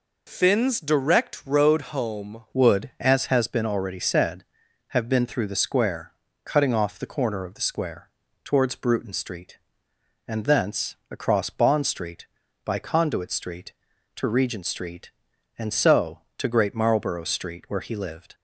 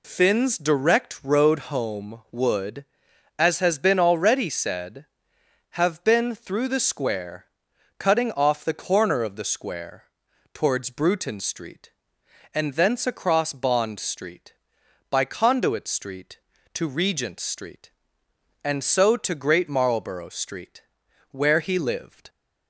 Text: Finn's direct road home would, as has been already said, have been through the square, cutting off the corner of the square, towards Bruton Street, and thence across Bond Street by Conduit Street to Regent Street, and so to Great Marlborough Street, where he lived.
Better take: second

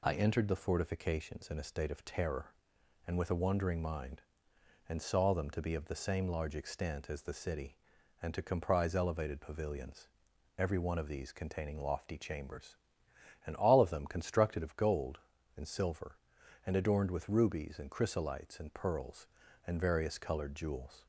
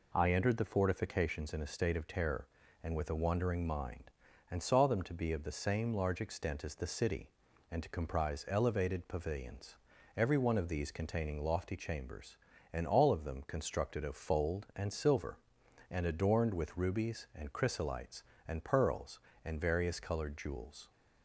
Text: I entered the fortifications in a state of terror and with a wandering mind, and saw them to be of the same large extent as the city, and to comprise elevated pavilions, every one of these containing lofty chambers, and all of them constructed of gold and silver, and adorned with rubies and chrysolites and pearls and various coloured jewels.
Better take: first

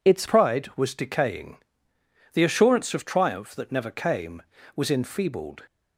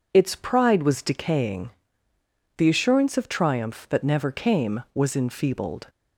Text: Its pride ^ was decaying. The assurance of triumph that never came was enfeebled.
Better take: second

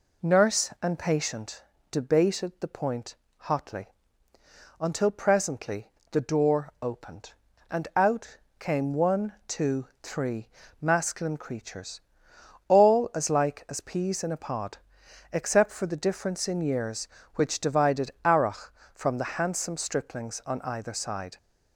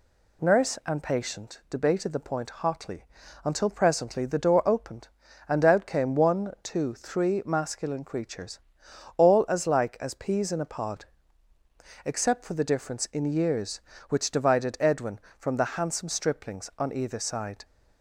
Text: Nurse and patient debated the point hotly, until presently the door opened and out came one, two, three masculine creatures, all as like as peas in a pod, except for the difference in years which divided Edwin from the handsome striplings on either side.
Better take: second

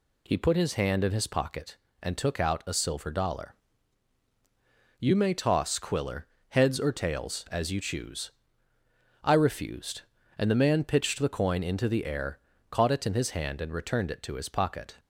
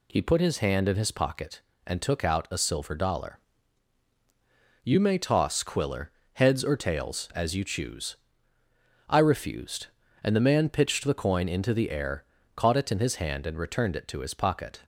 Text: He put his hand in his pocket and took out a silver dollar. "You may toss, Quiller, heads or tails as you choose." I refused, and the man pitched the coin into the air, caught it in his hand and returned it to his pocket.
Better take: neither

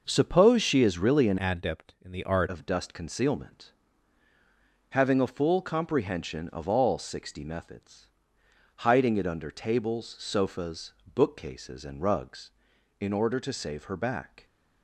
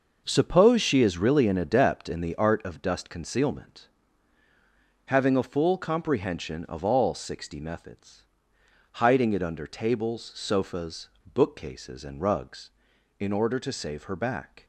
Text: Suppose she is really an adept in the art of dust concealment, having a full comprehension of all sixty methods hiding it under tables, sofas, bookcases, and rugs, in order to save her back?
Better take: second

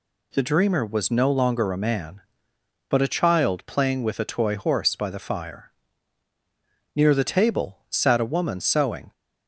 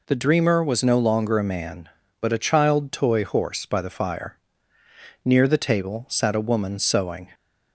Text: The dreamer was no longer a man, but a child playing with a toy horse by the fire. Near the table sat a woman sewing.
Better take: first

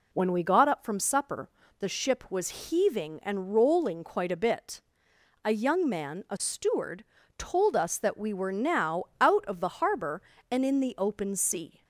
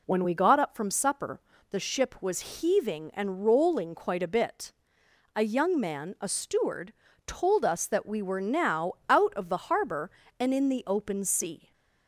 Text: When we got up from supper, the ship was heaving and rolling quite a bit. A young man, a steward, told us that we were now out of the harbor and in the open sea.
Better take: neither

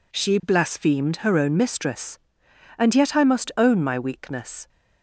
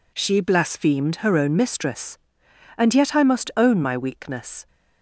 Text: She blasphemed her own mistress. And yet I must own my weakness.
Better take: neither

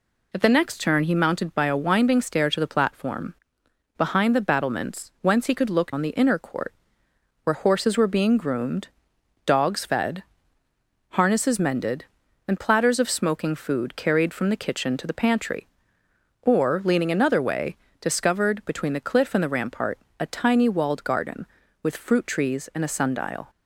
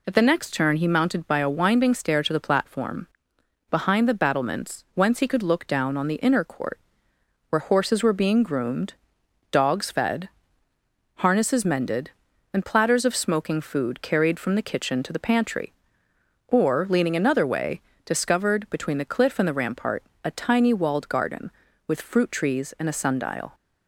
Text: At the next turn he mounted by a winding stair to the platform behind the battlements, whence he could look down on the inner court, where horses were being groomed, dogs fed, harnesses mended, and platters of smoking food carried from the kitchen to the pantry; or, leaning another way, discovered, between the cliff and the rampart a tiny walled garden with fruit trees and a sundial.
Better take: second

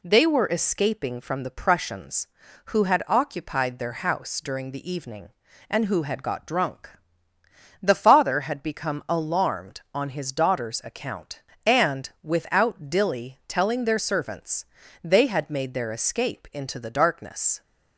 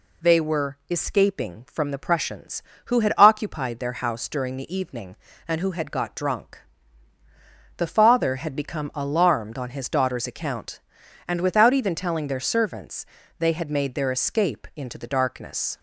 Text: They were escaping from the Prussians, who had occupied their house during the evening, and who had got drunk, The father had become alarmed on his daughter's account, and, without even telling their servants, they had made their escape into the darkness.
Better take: second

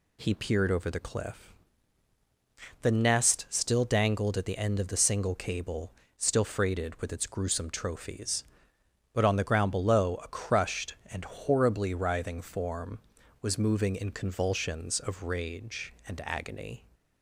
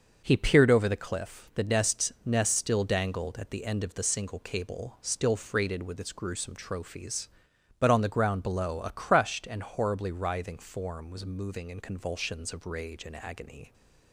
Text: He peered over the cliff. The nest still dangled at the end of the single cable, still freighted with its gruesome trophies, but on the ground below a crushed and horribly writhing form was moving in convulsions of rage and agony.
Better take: first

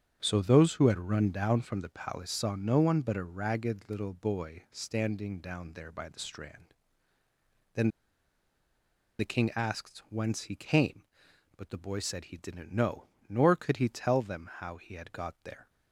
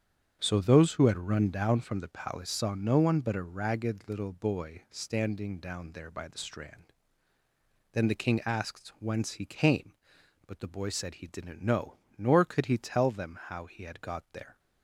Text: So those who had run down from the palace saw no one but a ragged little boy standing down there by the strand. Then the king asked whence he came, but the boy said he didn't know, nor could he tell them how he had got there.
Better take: second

